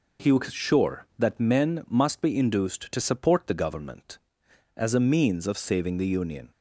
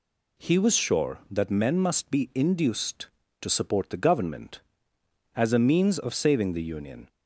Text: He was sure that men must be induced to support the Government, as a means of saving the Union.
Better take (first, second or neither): neither